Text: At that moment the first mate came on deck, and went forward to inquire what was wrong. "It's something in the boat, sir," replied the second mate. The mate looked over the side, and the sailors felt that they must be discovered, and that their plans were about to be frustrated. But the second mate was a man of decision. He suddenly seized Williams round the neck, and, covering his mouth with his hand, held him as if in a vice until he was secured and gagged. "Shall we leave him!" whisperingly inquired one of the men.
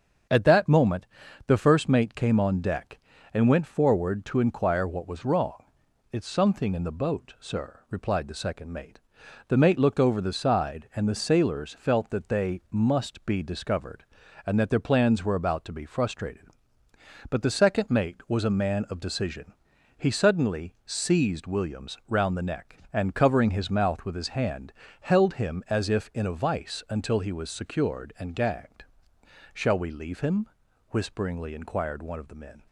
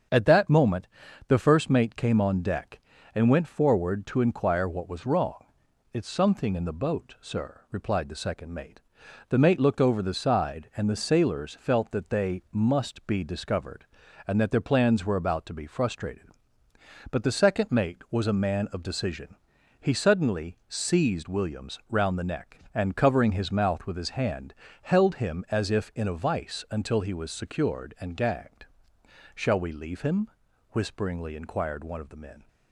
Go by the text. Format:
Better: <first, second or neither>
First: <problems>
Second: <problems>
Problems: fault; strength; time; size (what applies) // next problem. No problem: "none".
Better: neither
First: starts louder than the rest; strong; until 1.7 s; 7 dB // pauses between "moment" and "the"; at 1.0 s; 0.40 s long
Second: starts louder than the rest; strong; until 1.5 s; 7 dB // pauses between "moment" and "the"; at 0.8 s; 0.40 s long